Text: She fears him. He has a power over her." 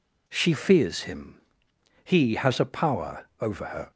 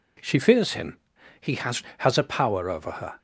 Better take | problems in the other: first | says "has" twice; at 1.9 s

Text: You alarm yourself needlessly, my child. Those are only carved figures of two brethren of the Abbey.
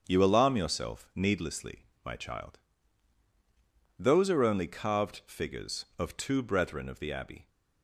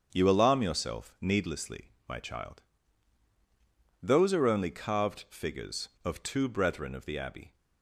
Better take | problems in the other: neither | starts louder than the rest; the same in both

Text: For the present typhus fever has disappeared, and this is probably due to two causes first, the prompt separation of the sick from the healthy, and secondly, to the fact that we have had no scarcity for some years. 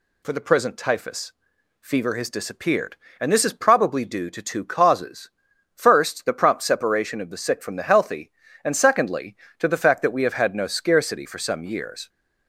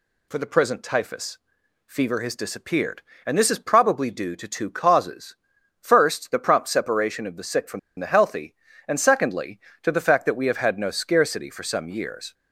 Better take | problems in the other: first | pauses between "typhus" and "fever"; noticeable; at 1.3 s; 0.48 s long; noticeable in the first // pauses between "causes" and "first"; noticeable; at 5.3 s; 0.46 s long; noticeable in the first // pauses between "from" and "the"; slight; at 7.7 s; 0.19 s long

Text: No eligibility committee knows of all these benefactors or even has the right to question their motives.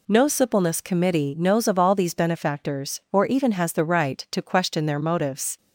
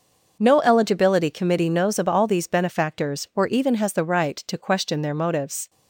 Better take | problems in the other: second | says "suppleness" for "eligibility"; at 0.2 s

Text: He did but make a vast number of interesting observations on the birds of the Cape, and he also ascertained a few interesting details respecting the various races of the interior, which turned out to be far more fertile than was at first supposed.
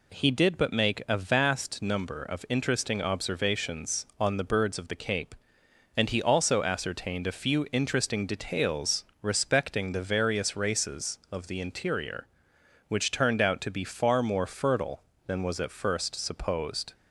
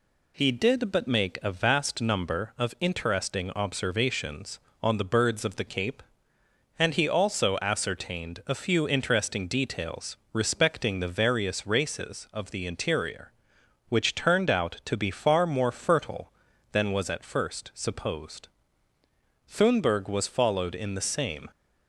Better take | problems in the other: first | pauses between "details" and "respecting"; slight; at 10.1 s; 0.16 s long; slight in the first // goes on to say "Thunberg was followed in the same"; strong; from 19.4 s on; 1.9 s long

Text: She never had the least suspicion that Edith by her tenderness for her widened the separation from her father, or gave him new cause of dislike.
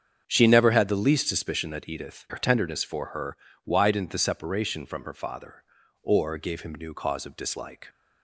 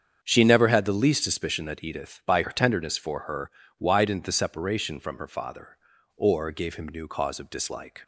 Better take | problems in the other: second | starts louder than the rest; strong; until 1.2 s; 7.5 dB; strong in the second // skips "by"; at 2.2 s // pauses between "her" and "widened"; slight; at 3.3 s; 0.28 s long; slight in the second

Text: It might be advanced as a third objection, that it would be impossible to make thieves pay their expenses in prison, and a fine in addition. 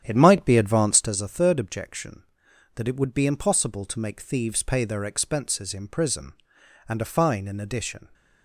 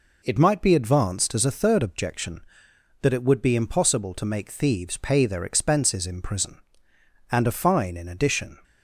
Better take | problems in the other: second | starts louder than the rest; strong; until 1.1 s; 9.5 dB

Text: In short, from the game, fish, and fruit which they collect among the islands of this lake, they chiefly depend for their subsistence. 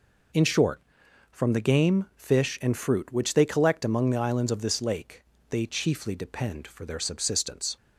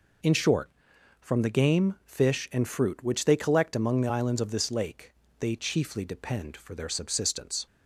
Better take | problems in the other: neither | none

